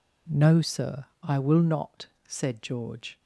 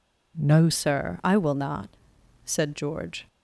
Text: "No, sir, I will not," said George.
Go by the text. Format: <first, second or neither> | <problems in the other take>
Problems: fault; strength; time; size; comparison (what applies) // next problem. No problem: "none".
first | changes voice at "sir"; from 0.7 s on; 2.5 s long